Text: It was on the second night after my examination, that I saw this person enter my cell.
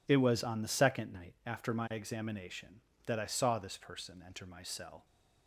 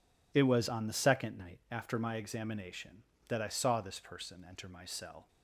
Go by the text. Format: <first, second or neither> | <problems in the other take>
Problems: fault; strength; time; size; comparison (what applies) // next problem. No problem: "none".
neither | none